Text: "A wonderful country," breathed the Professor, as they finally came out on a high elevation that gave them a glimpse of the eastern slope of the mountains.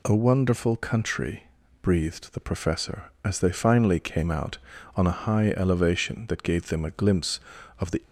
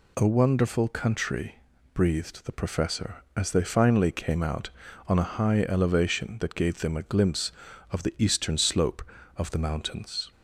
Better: second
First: stops before "eastern slope of the mountains"; at 8.0 s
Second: none

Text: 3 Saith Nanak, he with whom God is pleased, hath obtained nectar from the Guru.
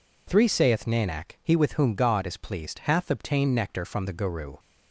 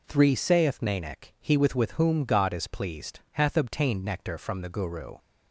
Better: first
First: none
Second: says "with" twice; at 1.7 s

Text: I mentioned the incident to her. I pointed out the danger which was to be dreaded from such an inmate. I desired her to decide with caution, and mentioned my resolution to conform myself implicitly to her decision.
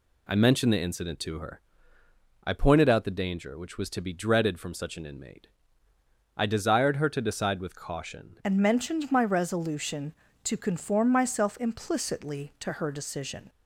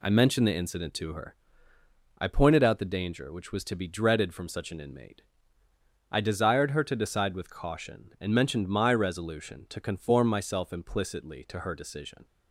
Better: second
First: changes voice at "and"; from 8.4 s on; 5.0 s long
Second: none

